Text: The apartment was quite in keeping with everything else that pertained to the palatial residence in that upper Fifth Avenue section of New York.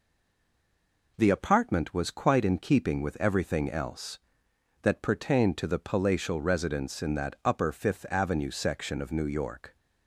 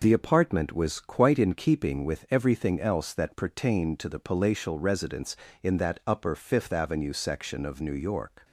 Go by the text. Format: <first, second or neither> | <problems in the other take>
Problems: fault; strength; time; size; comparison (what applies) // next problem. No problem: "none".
second | stays silent before the first word; until 1.1 s; 1.1 s long